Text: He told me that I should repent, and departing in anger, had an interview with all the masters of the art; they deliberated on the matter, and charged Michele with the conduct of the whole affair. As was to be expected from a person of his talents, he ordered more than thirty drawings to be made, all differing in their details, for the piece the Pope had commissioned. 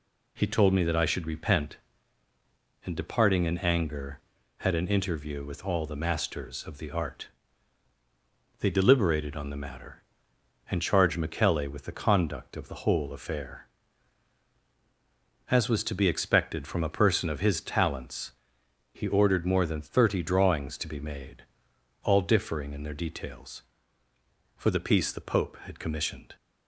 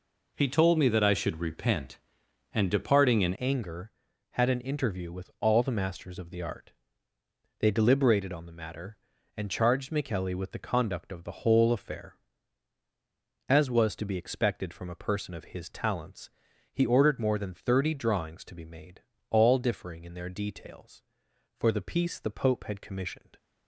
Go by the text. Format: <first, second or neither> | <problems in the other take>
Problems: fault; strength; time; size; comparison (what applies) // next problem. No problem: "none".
first | changes voice at "anger"; from 3.3 s on; 20.0 s long